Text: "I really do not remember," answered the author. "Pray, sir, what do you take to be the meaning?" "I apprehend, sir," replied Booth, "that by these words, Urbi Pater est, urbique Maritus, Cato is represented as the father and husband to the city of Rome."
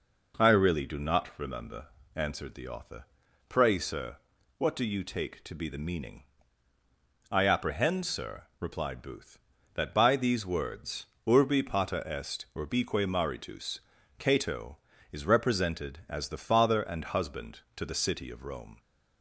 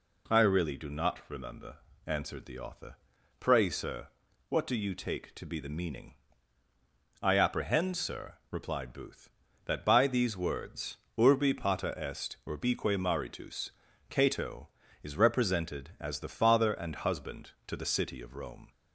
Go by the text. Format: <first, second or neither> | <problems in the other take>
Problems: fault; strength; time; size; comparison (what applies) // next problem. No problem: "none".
second | starts louder than the rest; noticeable; until 2.1 s; 4.5 dB